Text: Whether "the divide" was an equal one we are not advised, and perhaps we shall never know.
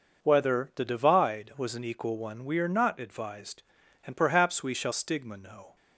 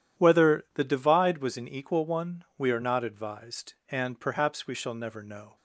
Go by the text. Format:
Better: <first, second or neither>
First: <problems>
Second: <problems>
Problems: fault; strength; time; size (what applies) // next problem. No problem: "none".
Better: second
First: says "stigma" for "never"; at 4.9 s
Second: none